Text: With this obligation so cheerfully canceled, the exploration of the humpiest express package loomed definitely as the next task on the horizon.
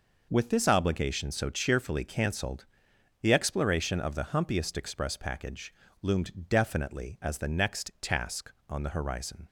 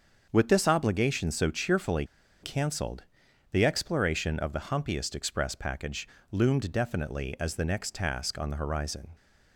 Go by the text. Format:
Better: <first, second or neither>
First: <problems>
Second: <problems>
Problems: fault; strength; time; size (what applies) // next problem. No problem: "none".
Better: first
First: pauses between "package" and "loomed"; slight; at 5.7 s; 0.29 s long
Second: starts louder than the rest; until 1.3 s; 6.5 dB // pauses between "cheerfully" and "canceled"; at 2.0 s; 0.38 s long // pauses between "package" and "loomed"; slight; at 6.0 s; 0.24 s long